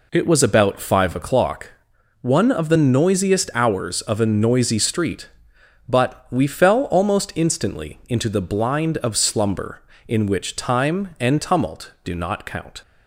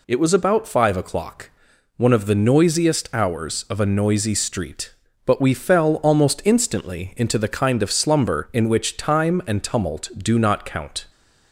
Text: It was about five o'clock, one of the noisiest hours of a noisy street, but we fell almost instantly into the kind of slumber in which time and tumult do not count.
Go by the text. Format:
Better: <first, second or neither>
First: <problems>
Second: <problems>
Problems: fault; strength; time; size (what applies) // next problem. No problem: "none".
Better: second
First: says "blind" for "kind"; at 8.4 s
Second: none